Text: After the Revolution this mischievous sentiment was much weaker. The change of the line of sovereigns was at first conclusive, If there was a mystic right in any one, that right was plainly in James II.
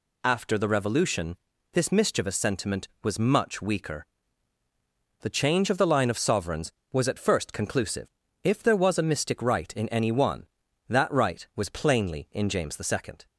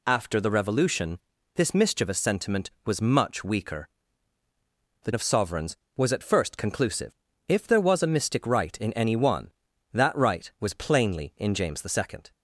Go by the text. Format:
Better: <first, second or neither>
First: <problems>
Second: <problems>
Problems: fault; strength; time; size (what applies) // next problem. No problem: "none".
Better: first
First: pauses between "Revolution" and "this"; slight; at 1.3 s; 0.36 s long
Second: pauses between "Revolution" and "this"; slight; at 1.1 s; 0.36 s long // skips "change of the line"; at 5.1 s